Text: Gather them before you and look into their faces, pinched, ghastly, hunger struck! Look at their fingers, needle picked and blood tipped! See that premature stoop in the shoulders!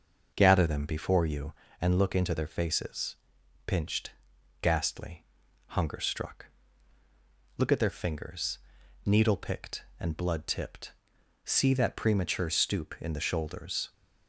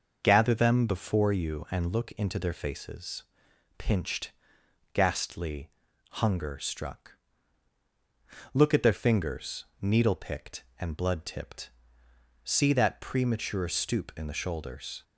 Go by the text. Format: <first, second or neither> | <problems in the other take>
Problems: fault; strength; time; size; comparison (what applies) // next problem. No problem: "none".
neither | starts louder than the rest; noticeable; the same in both